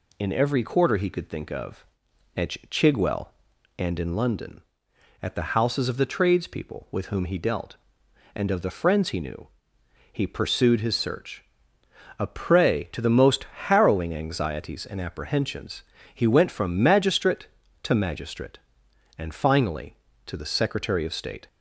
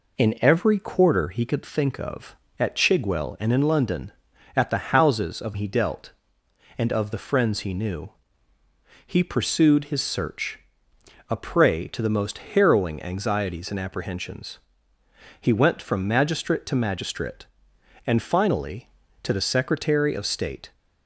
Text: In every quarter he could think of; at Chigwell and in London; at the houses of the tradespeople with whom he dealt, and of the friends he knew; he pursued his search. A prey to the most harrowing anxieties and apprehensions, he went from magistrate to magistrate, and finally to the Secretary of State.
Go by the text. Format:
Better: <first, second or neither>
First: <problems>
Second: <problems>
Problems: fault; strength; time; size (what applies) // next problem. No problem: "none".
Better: first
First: none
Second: skips "the tradespeople with whom"; at 5.5 s // pauses between "most" and "harrowing"; slight; at 12.3 s; 0.16 s long